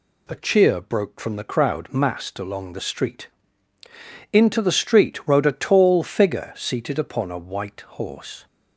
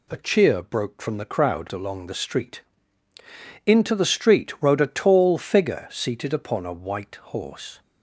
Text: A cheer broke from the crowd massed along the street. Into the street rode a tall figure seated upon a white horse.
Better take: first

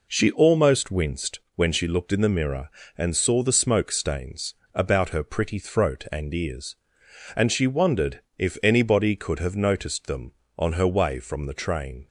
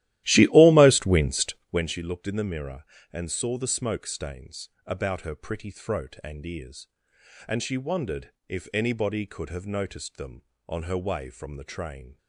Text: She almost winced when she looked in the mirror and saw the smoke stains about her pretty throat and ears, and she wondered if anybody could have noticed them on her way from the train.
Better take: first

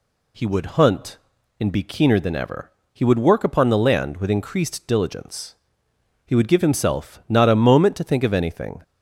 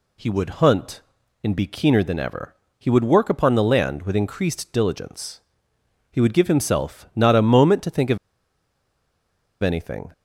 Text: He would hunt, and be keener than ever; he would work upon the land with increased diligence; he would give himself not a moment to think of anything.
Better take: first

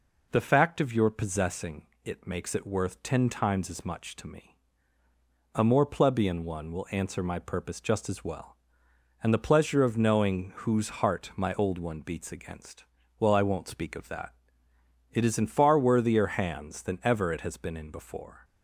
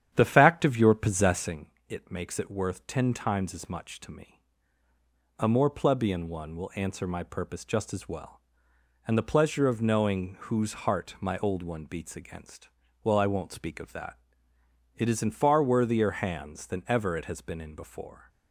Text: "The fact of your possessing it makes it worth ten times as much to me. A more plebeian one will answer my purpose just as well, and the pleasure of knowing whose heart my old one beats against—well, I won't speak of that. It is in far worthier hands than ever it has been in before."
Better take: first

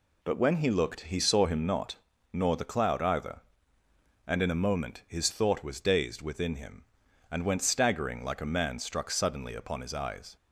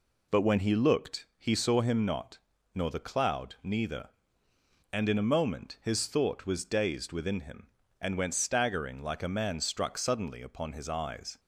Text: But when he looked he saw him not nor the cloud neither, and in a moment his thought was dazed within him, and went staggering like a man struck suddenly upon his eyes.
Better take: second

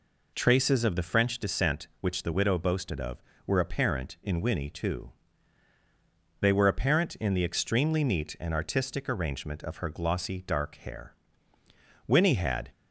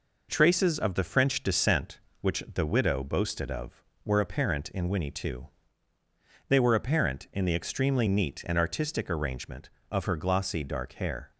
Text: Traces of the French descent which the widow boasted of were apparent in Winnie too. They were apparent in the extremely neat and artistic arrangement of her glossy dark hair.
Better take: second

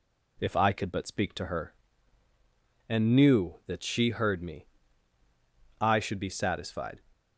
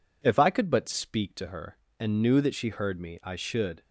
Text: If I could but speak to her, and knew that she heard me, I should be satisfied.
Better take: first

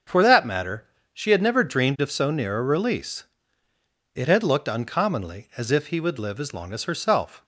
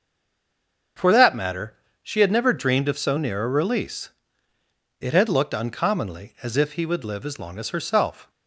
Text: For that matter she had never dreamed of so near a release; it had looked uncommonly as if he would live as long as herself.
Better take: first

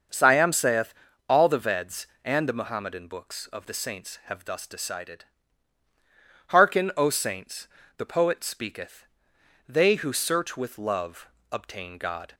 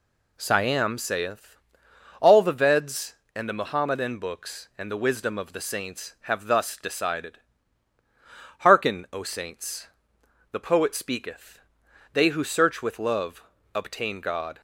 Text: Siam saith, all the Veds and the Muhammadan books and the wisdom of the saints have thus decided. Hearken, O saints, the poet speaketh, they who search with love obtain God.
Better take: second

